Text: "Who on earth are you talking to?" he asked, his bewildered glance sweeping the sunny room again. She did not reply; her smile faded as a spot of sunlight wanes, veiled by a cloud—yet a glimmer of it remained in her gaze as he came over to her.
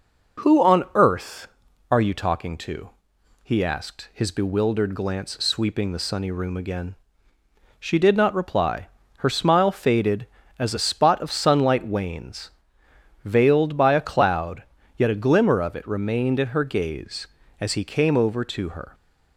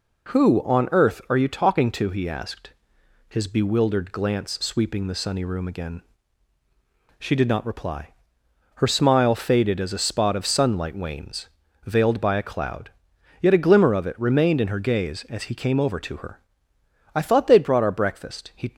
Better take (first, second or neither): first